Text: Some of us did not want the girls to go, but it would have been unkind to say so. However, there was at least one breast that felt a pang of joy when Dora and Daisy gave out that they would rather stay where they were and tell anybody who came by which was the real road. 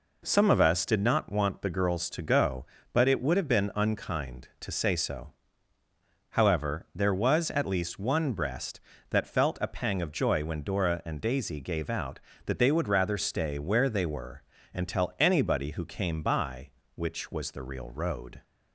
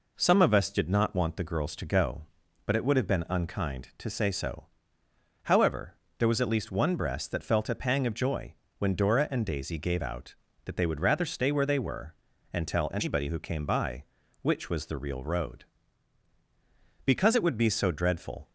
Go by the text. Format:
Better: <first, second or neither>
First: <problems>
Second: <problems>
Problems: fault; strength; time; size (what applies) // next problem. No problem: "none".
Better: first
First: none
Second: pauses between "joy" and "when"; slight; at 8.5 s; 0.26 s long // goes on to say "Because it would be so dreadful"; from 17.0 s on; 1.4 s long